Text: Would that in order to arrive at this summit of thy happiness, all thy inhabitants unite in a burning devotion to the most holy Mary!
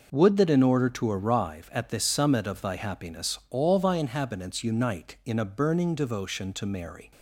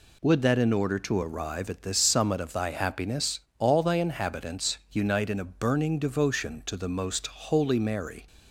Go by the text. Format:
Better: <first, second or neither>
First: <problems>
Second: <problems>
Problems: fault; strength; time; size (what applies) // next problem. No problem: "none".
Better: second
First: skips "the most holy"; at 6.6 s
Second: none